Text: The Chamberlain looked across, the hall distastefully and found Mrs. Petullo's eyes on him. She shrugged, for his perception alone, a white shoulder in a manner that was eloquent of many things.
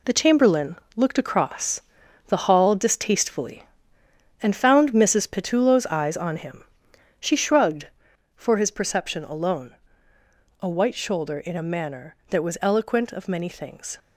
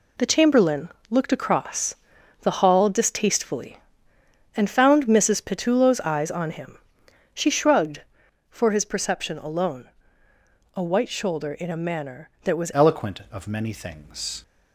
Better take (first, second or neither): first